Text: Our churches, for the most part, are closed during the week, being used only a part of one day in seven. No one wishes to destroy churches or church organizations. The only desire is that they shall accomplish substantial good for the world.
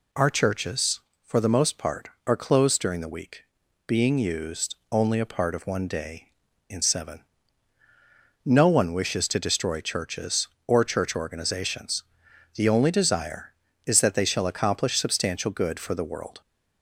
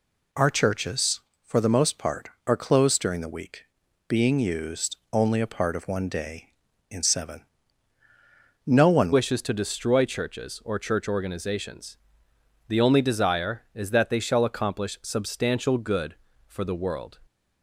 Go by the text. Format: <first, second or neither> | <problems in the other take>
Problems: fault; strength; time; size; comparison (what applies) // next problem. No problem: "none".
first | pauses between "used" and "only"; slight; at 4.9 s; 0.16 s long; slight in the first // changes voice at "wishes"; from 9.1 s on; 8.0 s long